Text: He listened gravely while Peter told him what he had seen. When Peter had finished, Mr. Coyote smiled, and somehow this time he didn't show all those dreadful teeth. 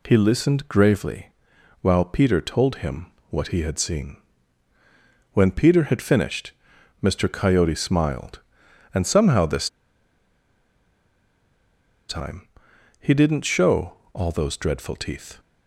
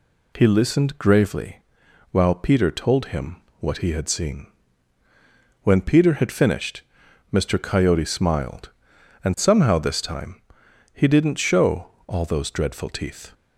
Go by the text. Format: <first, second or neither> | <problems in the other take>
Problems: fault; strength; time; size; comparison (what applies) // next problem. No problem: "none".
second | pauses between "gravely" and "while"; noticeable; at 1.2 s; 0.54 s long; noticeable in the second // pauses between "him" and "what"; slight; at 3.0 s; 0.24 s long; slight in the second // pauses between "this" and "time"; strong; at 9.6 s; 2.4 s long // pauses between "time" and "he"; noticeable; at 12.4 s; 0.52 s long; noticeable in the second // pauses between "show" and "all"; slight; at 13.9 s; 0.20 s long; slight in the second